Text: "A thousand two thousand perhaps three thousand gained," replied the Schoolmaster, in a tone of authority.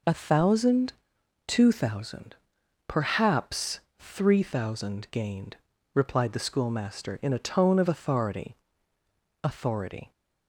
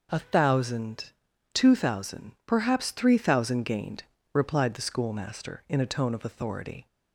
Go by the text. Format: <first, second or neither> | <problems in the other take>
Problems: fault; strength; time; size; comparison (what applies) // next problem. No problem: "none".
second | pauses between "thousand" and "two"; noticeable; at 0.9 s; 0.56 s long; also in the second // pauses between "thousand" and "perhaps"; noticeable; at 2.3 s; 0.52 s long; slight in the second // pauses between "perhaps" and "three"; slight; at 3.7 s; 0.18 s long // says "authority" twice; at 9.4 s